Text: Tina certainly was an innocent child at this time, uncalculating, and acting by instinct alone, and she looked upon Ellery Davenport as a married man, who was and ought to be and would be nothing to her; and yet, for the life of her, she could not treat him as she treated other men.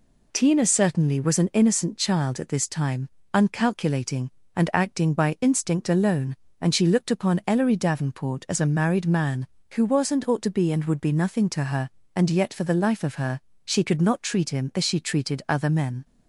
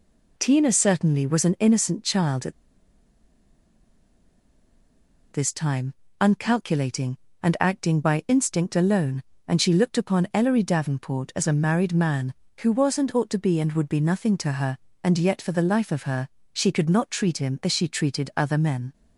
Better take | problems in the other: first | pauses between "at" and "this"; strong; at 2.5 s; 2.8 s long

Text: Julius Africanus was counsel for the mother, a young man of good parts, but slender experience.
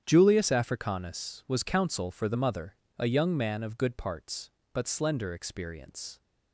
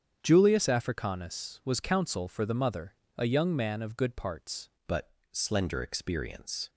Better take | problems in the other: first | starts louder than the rest; strong; until 1.2 s; 8 dB; strong in the first // changes voice at "but"; from 4.8 s on; 1.8 s long // pauses between "but" and "slender"; slight; at 5.1 s; 0.20 s long

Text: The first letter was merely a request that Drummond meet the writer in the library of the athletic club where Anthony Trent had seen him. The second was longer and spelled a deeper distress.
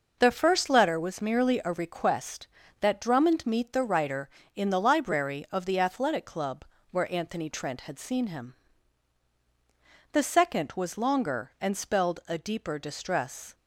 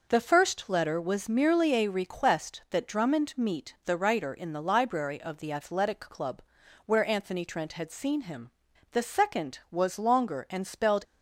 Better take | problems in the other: first | pauses between "club" and "where"; at 6.4 s; 0.42 s long; slight in the first // stops before "a deeper distress"; at 11.0 s

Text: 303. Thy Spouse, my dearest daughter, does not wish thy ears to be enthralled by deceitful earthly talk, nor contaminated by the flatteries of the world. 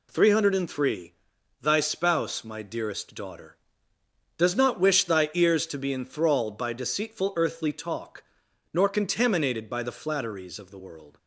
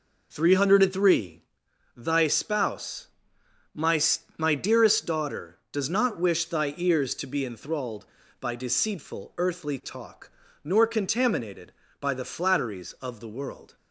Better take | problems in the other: first | says "my" twice; at 4.3 s

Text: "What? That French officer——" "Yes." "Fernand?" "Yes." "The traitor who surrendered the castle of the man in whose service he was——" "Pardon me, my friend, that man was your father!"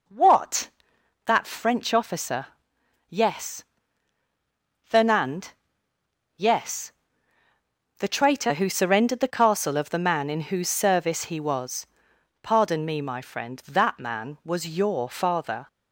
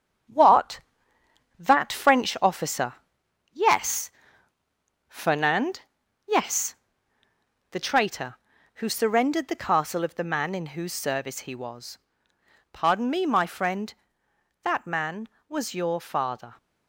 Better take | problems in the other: first | gets quieter; noticeable; throughout; 6 dB

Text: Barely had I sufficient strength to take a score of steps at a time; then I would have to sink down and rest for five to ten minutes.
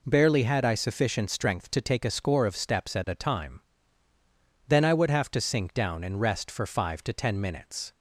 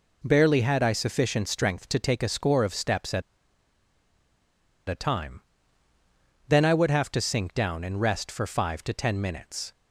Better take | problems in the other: first | pauses between "at" and "a"; strong; at 3.2 s; 1.6 s long

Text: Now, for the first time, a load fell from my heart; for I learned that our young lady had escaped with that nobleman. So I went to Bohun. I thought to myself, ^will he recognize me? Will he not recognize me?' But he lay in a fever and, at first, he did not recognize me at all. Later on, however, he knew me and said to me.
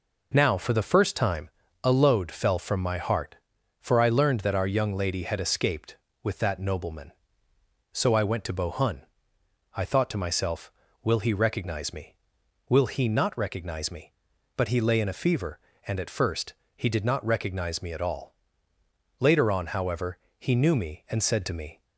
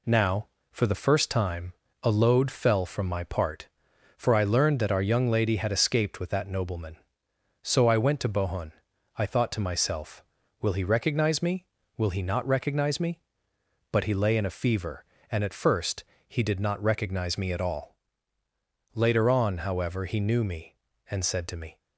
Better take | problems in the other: first | says "part" for "heart"; at 3.2 s

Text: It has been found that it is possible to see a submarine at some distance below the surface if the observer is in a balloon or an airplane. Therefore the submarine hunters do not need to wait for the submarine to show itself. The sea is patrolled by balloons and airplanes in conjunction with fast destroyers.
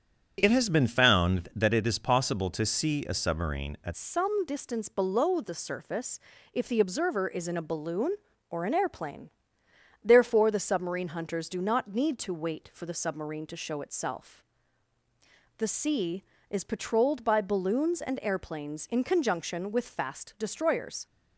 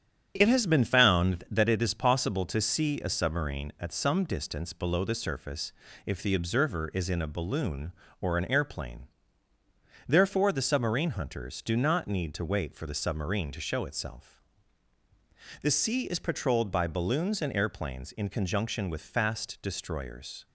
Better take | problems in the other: second | starts louder than the rest; strong; until 1.4 s; 8 dB; strong in the second // changes voice at "some"; from 3.9 s on; 17.1 s long // pauses between "surface" and "if"; slight; at 6.1 s; 0.36 s long; slight in the second

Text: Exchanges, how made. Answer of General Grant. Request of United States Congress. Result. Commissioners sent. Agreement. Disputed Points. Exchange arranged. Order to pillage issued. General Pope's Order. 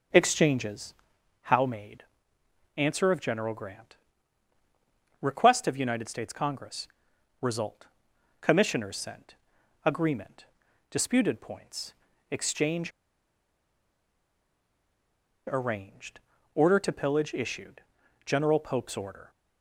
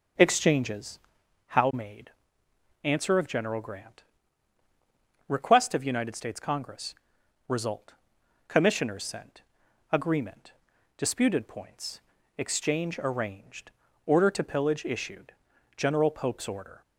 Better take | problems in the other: second | starts louder than the rest; until 1.6 s; 6.5 dB; also in the second // pauses between "Exchange" and "arranged"; strong; at 12.9 s; 2.5 s long

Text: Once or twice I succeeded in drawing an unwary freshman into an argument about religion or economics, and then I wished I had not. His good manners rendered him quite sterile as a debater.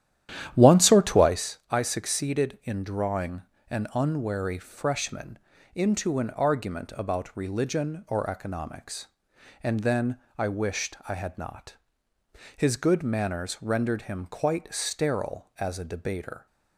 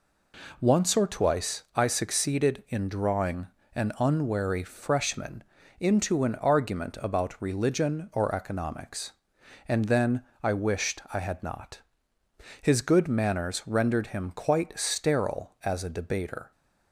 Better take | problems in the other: second | starts louder than the rest; strong; until 1.5 s; 11 dB // pauses between "drawing" and "an"; slight; at 3.4 s; 0.26 s long; slight in the second // pauses between "freshman" and "into"; slight; at 5.3 s; 0.34 s long; slight in the second // pauses between "then" and "I"; slight; at 10.1 s; 0.20 s long; slight in the second

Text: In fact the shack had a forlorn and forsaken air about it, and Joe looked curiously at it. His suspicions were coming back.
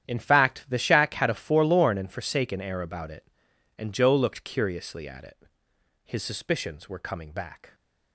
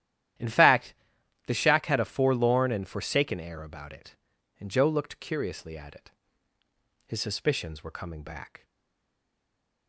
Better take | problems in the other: first | starts louder than the rest; strong; until 1.9 s; 12 dB; strong in the first // pauses between "fact" and "the"; noticeable; at 0.9 s; 0.52 s long // stays silent after the last word; noticeable; from 8.6 s on; 1.2 s long

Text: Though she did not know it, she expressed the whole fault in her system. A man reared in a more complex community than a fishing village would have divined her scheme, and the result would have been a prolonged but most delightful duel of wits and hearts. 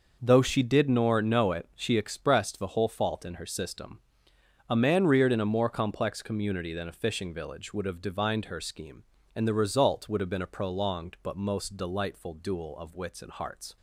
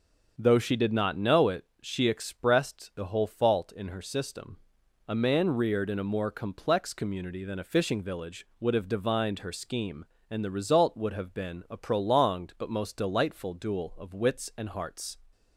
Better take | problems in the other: second | starts louder than the rest; noticeable; until 1.2 s; 6 dB; also in the second // says "nor" for "not"; at 0.8 s

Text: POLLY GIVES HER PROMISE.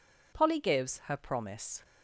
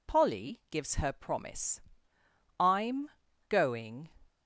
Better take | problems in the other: first | goes on to say "I'M going"; from 2.5 s on; 1.5 s long

